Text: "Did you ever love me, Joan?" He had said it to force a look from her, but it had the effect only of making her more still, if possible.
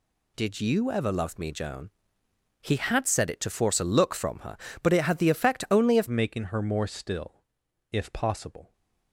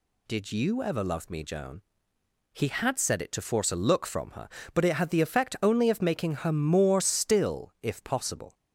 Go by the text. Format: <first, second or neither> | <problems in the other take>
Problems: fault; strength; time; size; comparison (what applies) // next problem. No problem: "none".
second | changes voice at "making"; from 6.0 s on; 2.7 s long